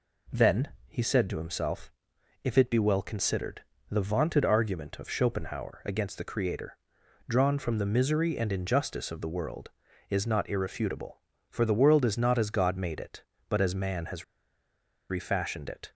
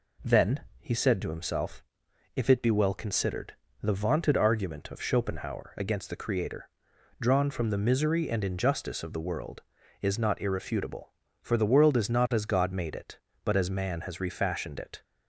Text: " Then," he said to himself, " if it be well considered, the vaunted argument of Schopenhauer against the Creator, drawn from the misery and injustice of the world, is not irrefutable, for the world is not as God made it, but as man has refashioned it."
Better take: second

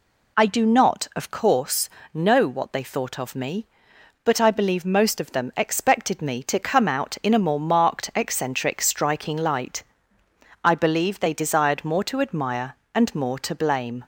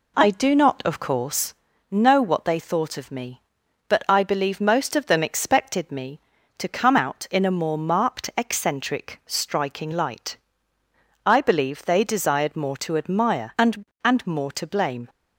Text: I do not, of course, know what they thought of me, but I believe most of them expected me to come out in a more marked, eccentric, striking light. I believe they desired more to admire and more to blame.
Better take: first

